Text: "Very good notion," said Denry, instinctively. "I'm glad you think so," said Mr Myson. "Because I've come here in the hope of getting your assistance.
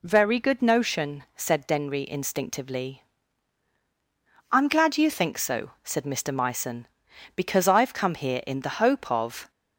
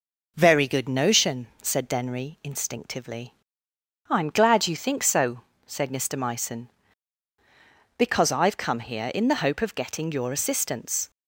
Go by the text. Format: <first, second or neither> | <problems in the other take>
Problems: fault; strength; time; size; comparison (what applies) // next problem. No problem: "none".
second | stops before "getting your assistance"; at 9.5 s